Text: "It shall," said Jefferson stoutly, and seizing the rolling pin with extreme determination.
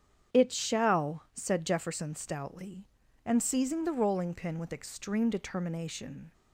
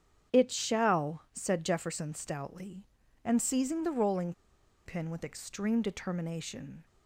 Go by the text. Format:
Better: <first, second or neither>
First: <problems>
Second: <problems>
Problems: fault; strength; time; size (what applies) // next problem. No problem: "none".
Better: first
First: starts louder than the rest; strong; until 1.4 s; 8.5 dB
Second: starts louder than the rest; strong; until 1.4 s; 8.5 dB // pauses between "rolling" and "pin"; noticeable; at 4.3 s; 0.54 s long